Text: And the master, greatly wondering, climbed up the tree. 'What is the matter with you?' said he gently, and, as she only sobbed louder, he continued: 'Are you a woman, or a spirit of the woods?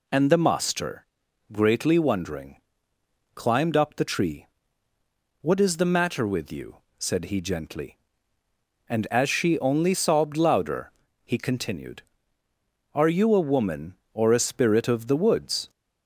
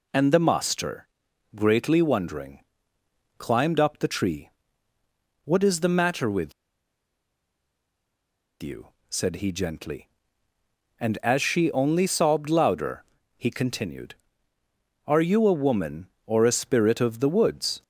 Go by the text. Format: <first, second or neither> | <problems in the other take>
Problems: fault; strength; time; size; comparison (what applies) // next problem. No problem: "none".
first | pauses between "with" and "you"; strong; at 6.5 s; 2.0 s long